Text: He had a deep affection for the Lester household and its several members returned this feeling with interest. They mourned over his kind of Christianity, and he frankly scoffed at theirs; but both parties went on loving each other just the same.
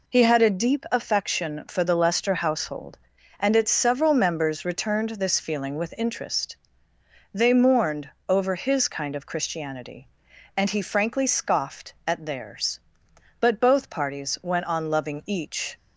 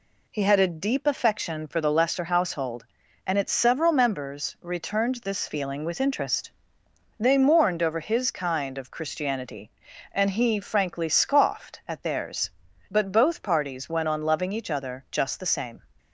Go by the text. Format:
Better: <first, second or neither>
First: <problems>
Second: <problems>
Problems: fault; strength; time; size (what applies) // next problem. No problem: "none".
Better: second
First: pauses between "mourned" and "over"; slight; at 8.0 s; 0.20 s long // stops before "other just the same"; at 15.7 s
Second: none